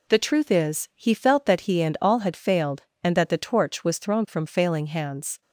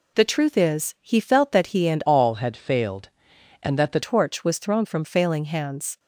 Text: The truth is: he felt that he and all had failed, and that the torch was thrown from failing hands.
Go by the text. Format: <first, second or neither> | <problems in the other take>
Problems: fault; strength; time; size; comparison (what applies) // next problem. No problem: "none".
first | changes voice from "all" to "the"; from 2.0 to 4.0 s; 2.0 s long